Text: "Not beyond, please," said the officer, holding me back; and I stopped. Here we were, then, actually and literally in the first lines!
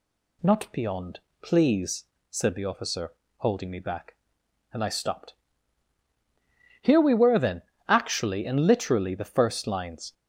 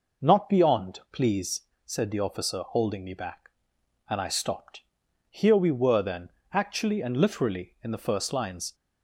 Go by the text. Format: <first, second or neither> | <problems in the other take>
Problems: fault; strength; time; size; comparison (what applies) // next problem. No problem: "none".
second | skips "in"; at 9.1 s